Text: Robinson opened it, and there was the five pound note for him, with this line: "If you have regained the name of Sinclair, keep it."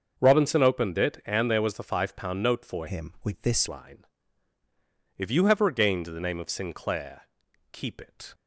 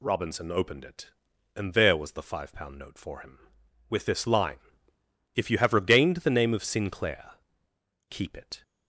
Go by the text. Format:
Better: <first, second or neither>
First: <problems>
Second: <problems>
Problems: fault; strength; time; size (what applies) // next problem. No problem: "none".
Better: second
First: starts louder than the rest; until 1.1 s; 6.5 dB // changes voice from "him" to "this"; from 2.8 to 3.6 s; 0.8 s long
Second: none